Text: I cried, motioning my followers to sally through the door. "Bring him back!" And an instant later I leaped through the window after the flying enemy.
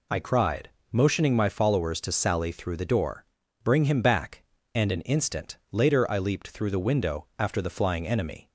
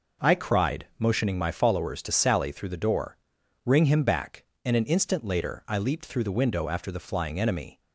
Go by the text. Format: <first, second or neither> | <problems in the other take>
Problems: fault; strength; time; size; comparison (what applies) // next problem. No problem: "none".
first | says "Ring" for "Bring"; at 3.6 s